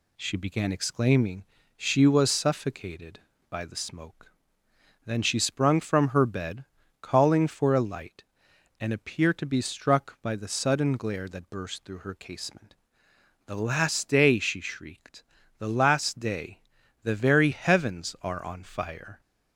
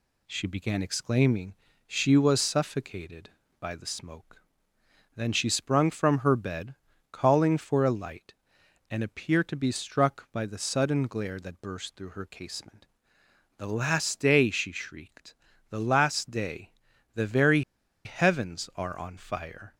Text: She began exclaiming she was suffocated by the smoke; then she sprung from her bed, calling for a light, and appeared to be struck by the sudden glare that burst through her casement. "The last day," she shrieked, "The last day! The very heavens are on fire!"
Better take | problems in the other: first | pauses between "exclaiming" and "she"; slight; at 1.5 s; 0.32 s long; slight in the first // pauses between "very" and "heavens"; at 17.6 s; 0.44 s long

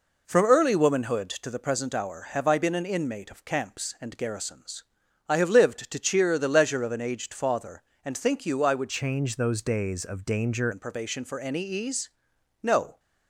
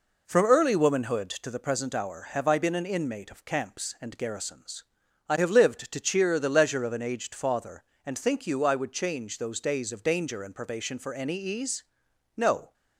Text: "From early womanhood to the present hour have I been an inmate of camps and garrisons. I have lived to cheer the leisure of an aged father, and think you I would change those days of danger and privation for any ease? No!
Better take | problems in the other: second | changes voice from "change" to "danger"; from 8.8 to 10.6 s; 1.8 s long

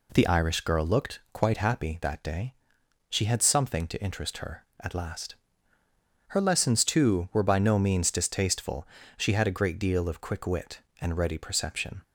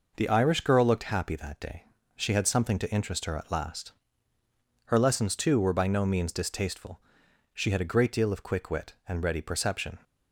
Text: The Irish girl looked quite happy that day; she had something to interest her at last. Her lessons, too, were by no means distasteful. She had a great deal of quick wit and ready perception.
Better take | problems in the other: first | skips "quite"; at 1.0 s

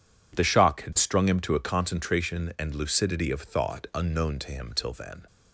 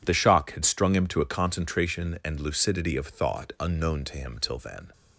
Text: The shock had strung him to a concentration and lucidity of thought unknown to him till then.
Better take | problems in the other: neither | none

